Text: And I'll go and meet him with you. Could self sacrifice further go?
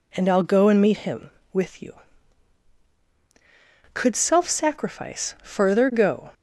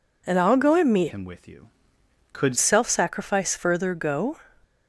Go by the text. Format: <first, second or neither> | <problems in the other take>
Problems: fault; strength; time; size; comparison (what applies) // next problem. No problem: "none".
first | changes voice from "him" to "Could"; from 1.0 to 2.5 s; 1.5 s long